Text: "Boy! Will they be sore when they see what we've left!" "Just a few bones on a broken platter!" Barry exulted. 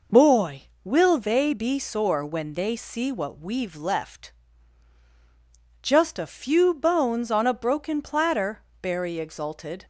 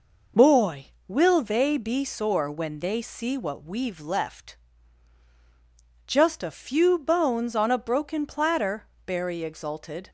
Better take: neither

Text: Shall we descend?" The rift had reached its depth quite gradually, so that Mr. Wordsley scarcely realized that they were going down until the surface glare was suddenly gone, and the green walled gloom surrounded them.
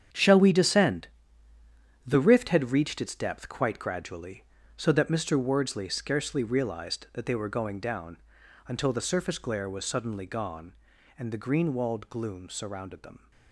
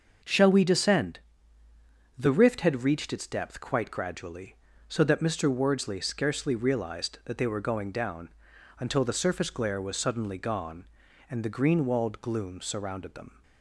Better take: second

